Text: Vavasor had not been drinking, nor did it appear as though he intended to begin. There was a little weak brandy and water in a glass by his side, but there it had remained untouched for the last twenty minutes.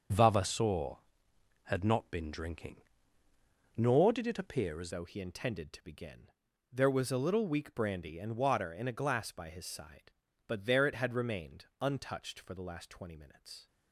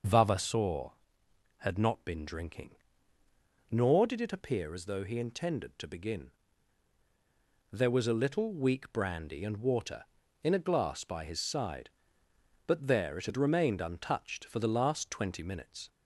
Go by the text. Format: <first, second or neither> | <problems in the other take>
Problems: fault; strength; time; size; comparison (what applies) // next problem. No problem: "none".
second | starts louder than the rest; until 1.7 s; 7 dB; noticeable in the second // changes voice at "though"; from 4.9 s on; 8.7 s long // pauses between "remained" and "untouched"; slight; at 11.6 s; 0.16 s long